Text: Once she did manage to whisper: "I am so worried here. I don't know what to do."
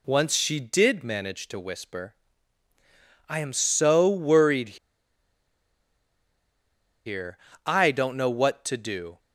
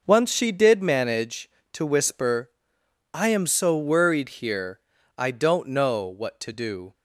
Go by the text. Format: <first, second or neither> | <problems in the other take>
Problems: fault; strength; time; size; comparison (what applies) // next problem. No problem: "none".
second | pauses between "worried" and "here"; strong; at 4.7 s; 2.2 s long